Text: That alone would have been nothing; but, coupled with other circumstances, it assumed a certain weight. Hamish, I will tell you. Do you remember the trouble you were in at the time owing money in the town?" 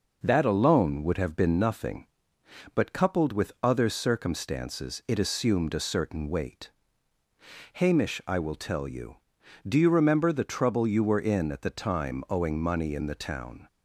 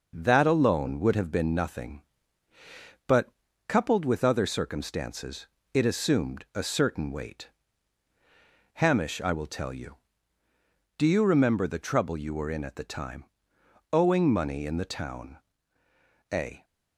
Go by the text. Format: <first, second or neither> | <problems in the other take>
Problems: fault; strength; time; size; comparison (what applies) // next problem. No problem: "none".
first | pauses between "time" and "owing"; noticeable; at 13.2 s; 0.68 s long // goes on to say "A"; slight; from 16.3 s on; 0.32 s long